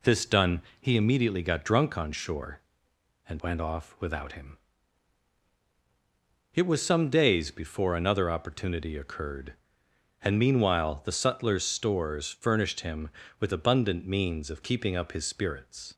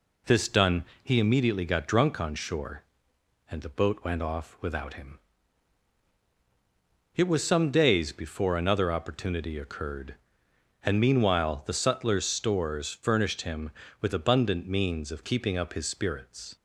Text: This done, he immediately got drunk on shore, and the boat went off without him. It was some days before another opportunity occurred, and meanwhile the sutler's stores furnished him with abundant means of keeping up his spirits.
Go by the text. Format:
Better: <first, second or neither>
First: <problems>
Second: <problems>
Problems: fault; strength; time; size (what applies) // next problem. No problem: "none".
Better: second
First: skips "the boat"; at 3.4 s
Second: none